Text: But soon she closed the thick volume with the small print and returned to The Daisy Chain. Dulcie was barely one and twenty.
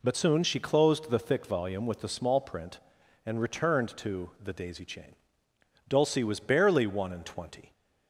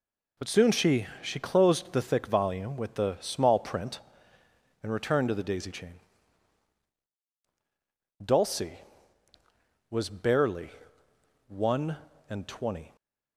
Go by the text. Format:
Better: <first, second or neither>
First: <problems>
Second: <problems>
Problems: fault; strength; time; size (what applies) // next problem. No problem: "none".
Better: first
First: none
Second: says "she" twice; at 1.2 s // pauses between "barely" and "one"; noticeable; at 10.6 s; 0.78 s long